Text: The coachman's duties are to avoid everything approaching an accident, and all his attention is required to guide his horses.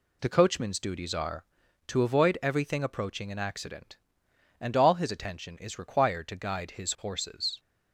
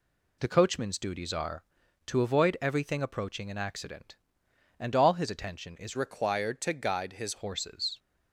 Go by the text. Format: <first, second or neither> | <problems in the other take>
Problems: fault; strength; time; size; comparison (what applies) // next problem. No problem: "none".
first | changes voice from "required" to "his"; from 5.9 to 7.3 s; 1.4 s long